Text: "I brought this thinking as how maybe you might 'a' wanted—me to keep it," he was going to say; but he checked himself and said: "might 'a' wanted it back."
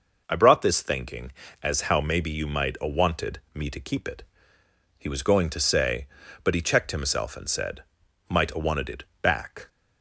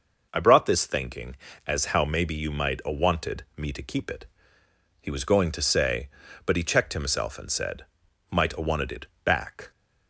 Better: neither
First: pauses between "it" and "back"; slight; at 9.0 s; 0.16 s long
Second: pauses between "it" and "back"; slight; at 9.0 s; 0.16 s long

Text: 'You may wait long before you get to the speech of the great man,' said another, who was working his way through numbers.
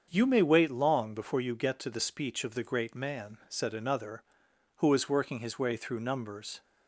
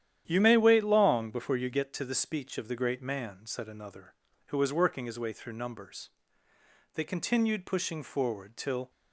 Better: first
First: starts louder than the rest; until 1.1 s; 7 dB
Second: starts louder than the rest; strong; until 1.2 s; 10.5 dB // goes on to say "They continued pushing forward till"; strong; from 6.9 s on; 1.9 s long

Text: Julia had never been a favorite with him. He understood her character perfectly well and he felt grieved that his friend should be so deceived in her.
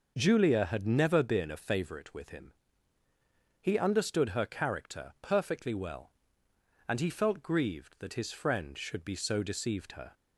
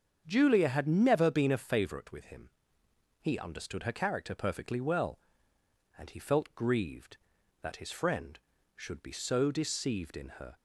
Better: second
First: starts louder than the rest; noticeable; until 1.1 s; 6 dB // skips "in"; at 9.9 s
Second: starts louder than the rest; strong; until 1.2 s; 7 dB

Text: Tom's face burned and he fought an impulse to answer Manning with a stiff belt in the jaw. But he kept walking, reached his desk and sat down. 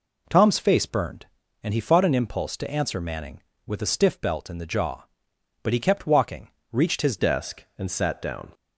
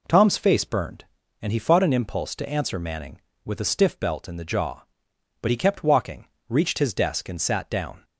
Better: second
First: changes voice at "desk"; from 7.1 s on; 1.4 s long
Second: none

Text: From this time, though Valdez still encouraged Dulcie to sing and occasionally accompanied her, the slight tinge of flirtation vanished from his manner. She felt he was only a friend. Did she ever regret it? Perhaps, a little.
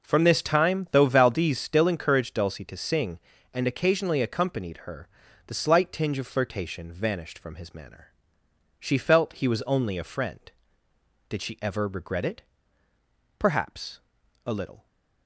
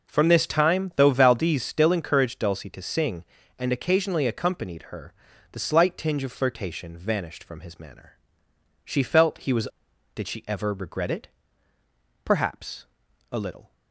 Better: first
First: none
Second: skips "only a friend"; at 9.9 s

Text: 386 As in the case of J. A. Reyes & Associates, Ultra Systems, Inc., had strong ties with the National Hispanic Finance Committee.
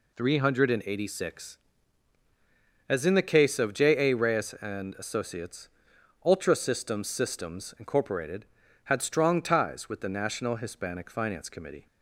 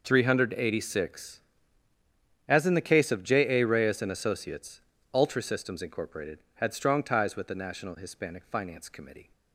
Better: second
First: says "Systems" twice; at 7.0 s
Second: none

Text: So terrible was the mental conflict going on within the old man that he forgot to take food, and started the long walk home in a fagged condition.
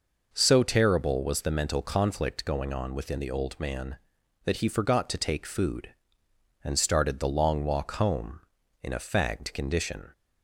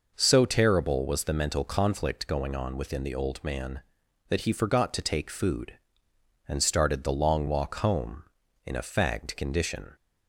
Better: neither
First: none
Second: none

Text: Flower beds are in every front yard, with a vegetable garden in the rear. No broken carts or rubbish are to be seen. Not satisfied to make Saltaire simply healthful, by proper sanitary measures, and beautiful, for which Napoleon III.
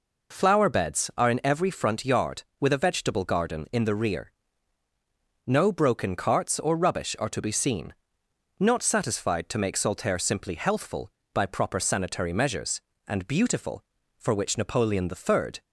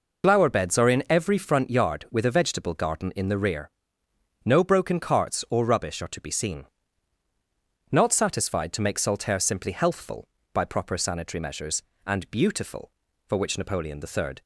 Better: first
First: none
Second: loses the start of "Flower"; at 0.2 s; 60 ms

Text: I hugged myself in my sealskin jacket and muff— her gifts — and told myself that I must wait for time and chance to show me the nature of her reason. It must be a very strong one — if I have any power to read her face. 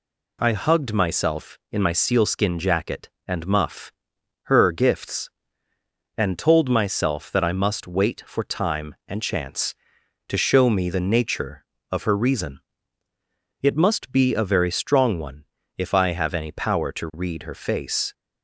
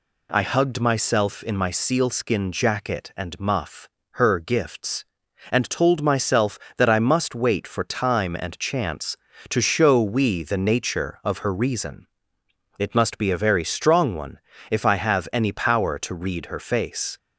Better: first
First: none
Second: says "we" for "me"; at 10.0 s

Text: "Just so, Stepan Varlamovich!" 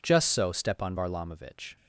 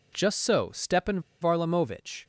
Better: first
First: none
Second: pauses between "Stepan" and "Varlamovich"; slight; at 1.1 s; 0.21 s long

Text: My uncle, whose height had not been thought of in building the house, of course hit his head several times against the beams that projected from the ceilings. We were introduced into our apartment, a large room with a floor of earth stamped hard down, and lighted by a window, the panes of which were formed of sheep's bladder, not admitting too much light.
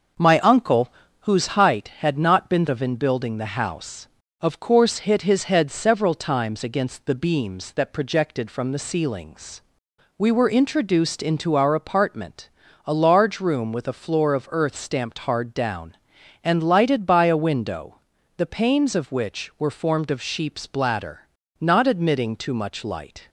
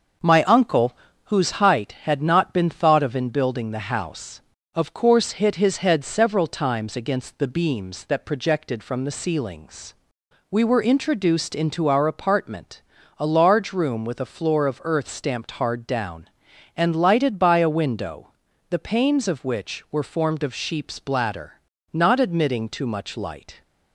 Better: second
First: starts louder than the rest; noticeable; until 1.5 s; 6 dB // skips "thought"; at 2.6 s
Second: starts louder than the rest; noticeable; until 1.5 s; 6 dB

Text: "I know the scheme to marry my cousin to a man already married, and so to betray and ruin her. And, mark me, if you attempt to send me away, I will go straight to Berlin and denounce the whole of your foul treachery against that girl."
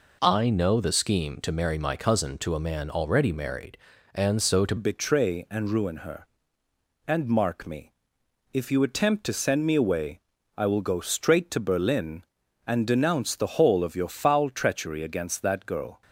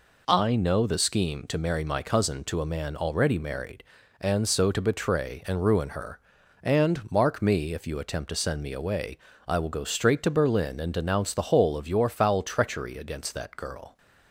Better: second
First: changes voice at "betray"; from 4.7 s on; 11.3 s long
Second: none

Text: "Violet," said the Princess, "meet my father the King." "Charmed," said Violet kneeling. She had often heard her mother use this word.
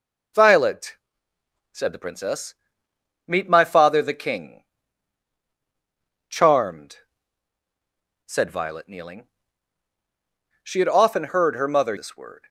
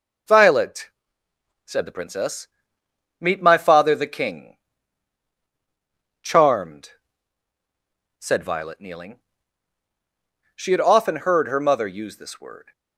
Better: second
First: skips "use"; at 11.9 s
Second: none

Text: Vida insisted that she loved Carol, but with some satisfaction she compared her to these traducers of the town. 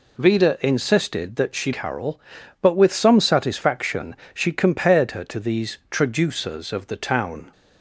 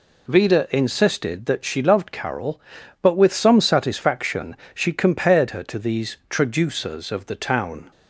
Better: second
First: skips "loved"; at 1.7 s // pauses between "satisfaction" and "she"; slight; at 4.1 s; 0.18 s long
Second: pauses between "satisfaction" and "she"; slight; at 4.5 s; 0.18 s long

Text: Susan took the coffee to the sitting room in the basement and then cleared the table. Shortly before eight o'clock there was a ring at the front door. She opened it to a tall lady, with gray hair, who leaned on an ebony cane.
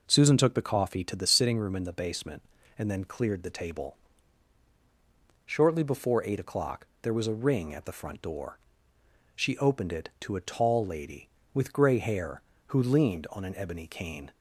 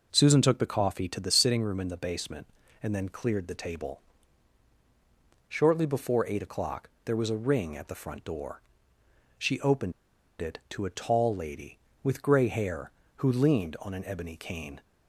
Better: first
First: pauses between "o'clock" and "there"; slight; at 6.8 s; 0.16 s long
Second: pauses between "o'clock" and "there"; slight; at 6.8 s; 0.16 s long // pauses between "opened" and "it"; noticeable; at 9.9 s; 0.49 s long

